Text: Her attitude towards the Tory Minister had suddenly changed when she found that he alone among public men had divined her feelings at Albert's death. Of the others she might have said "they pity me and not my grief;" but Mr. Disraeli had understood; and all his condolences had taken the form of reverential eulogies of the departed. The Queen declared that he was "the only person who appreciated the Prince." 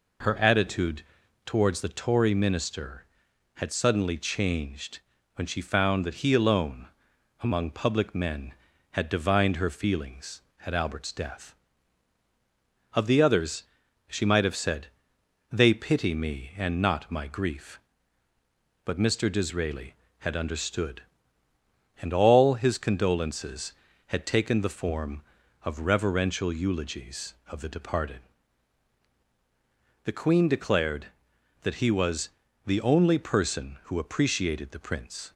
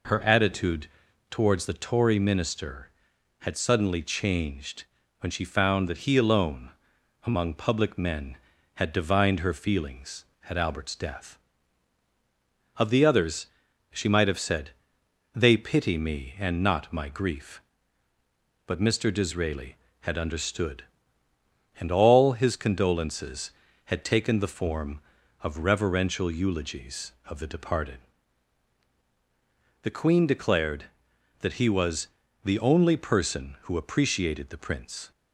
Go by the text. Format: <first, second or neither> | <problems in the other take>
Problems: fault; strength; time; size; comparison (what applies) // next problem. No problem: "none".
neither | pauses between "attitude" and "towards"; noticeable; the same in both // pauses between "changed" and "when"; slight; the same in both // pauses between "alone" and "among"; noticeable; the same in both // pauses between "others" and "she"; the same in both // pauses between "said" and "they"; noticeable; the same in both // pauses between "was" and "the"; the same in both